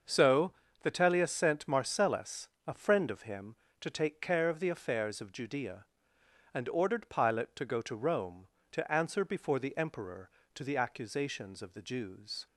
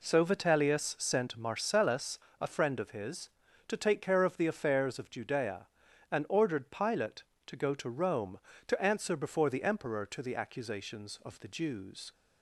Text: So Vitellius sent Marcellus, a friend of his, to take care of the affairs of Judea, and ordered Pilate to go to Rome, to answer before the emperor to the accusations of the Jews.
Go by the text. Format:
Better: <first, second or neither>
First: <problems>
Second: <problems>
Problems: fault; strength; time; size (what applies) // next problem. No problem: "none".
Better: second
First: starts louder than the rest; until 1.3 s; 6.5 dB // pauses between "So" and "Vitellius"; slight; at 0.5 s; 0.32 s long // says "him" for "his"; at 3.2 s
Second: none